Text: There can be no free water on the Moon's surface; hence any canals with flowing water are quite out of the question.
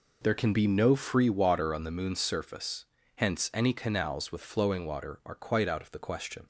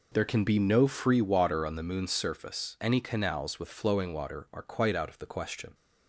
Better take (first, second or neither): first